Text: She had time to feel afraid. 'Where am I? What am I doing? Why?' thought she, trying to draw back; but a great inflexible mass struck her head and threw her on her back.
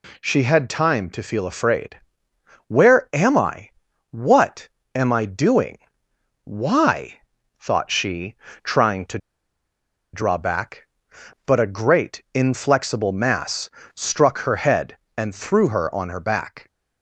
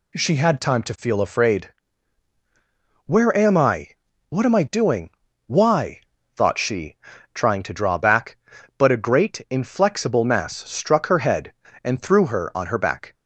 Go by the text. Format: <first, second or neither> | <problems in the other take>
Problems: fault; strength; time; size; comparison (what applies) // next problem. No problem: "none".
second | pauses between "What" and "am"; slight; at 4.6 s; 0.26 s long // pauses between "to" and "draw"; noticeable; at 9.1 s; 0.94 s long // pauses between "mass" and "struck"; slight; at 13.7 s; 0.24 s long; slight in the second